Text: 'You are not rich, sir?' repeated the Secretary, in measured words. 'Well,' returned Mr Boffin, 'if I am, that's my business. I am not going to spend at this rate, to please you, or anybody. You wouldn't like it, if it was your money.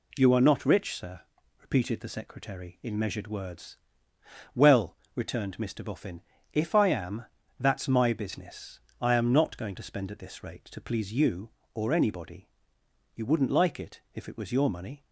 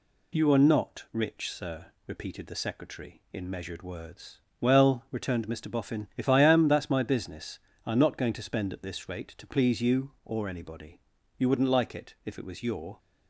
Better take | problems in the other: first | stops before "money"; at 12.9 s

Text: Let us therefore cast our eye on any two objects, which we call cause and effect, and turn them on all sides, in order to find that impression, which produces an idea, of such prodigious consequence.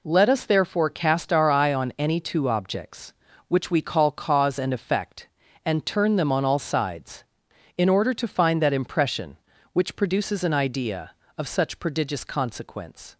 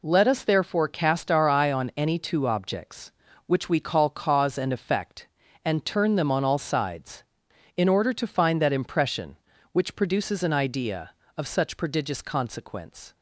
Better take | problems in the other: neither | none

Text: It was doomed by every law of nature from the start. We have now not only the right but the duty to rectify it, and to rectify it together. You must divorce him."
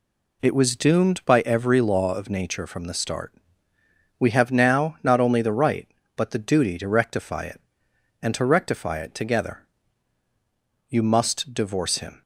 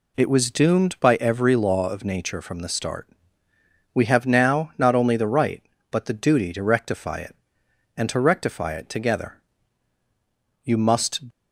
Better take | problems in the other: first | stops before "divorce him"; at 11.3 s

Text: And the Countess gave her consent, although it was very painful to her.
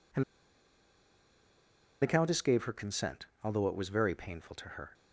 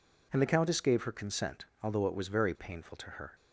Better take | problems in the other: second | pauses between "And" and "the"; strong; at 0.2 s; 1.7 s long

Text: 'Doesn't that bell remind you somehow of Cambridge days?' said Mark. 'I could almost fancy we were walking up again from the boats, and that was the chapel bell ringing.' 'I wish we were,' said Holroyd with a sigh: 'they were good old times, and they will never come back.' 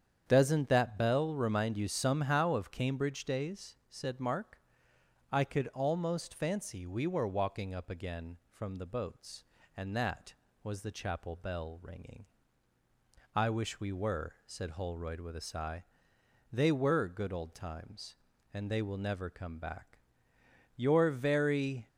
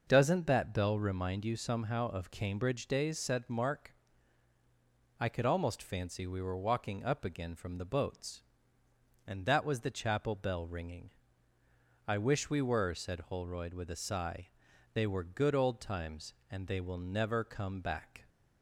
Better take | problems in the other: second | starts louder than the rest; strong; until 1.2 s; 8 dB // goes on to say "You're very"; noticeable; from 20.7 s on; 1.1 s long

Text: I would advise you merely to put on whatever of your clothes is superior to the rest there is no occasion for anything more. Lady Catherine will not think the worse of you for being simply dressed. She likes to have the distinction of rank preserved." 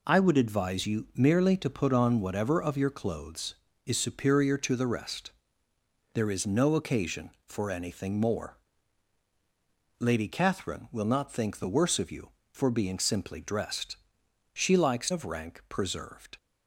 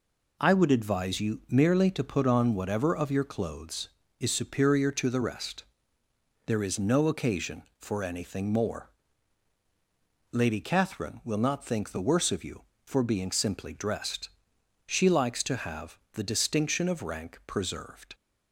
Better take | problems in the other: second | pauses between "rest" and "there"; noticeable; at 5.3 s; 0.80 s long; noticeable in the second // skips "to have the distinction"; at 15.1 s

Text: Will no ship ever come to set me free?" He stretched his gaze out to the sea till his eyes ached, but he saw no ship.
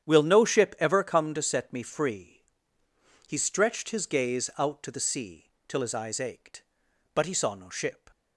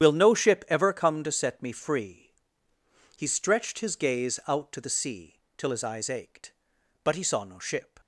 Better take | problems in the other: first | loses the start of "Will"; at 0.0 s; 70 ms // starts louder than the rest; strong; until 1.0 s; 9.5 dB; strong in the first // pauses between "sea" and "till"; slight; at 5.3 s; 0.18 s long; slight in the first

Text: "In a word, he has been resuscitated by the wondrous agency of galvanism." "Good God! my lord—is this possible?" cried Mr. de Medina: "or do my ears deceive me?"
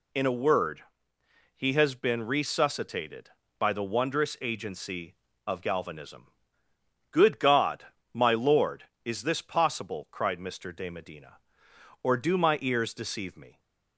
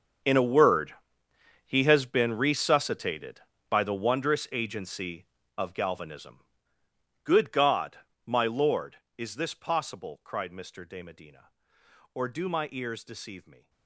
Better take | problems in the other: first | gets quieter; strong; throughout; 17.5 dB

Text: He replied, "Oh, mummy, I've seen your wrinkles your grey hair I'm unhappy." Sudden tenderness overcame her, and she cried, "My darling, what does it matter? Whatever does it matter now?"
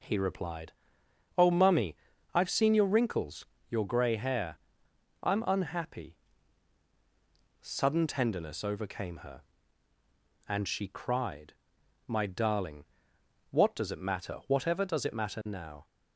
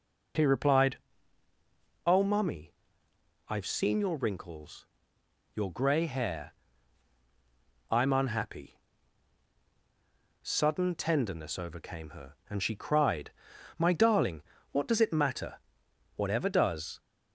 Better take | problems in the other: first | pauses between "wrinkles" and "your"; noticeable; at 4.8 s; 0.70 s long; slight in the first // pauses between "hair" and "I'm"; strong; at 6.5 s; 1.3 s long; noticeable in the first // stops before "it matter now"; at 16.9 s

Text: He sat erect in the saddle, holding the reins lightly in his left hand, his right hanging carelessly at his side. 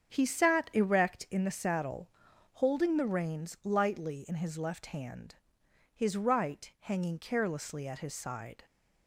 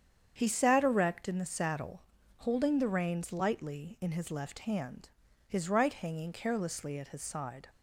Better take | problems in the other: neither | starts louder than the rest; strong; the same in both

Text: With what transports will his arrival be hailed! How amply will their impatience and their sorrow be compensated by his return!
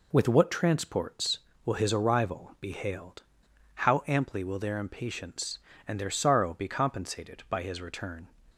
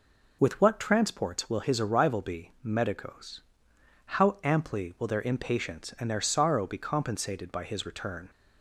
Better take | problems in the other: first | says "medicos" for "hailed"; at 2.6 s

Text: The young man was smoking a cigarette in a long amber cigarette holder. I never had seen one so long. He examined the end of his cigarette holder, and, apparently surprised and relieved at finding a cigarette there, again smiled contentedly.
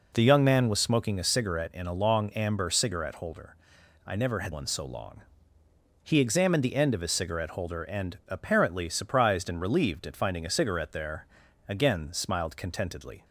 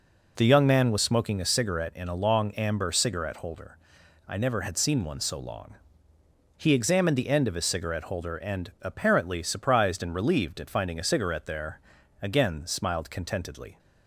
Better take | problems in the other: second | skips "seen"; at 4.5 s

